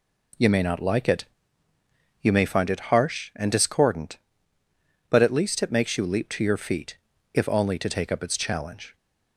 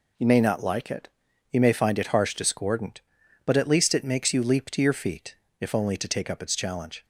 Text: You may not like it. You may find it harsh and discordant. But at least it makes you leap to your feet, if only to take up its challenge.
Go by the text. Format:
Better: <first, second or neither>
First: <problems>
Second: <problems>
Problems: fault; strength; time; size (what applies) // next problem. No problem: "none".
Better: first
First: none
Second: skips "and"; at 2.3 s